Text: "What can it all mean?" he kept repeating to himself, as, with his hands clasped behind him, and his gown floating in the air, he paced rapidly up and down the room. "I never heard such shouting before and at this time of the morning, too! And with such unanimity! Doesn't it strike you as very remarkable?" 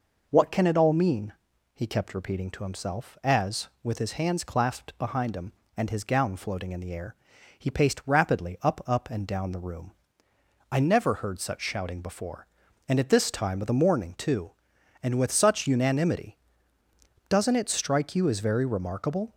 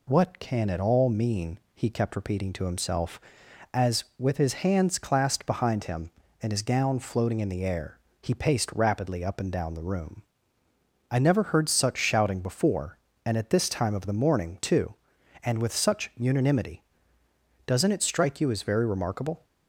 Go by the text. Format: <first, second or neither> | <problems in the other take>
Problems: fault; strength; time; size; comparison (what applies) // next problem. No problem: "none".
second | says "up" twice; at 8.8 s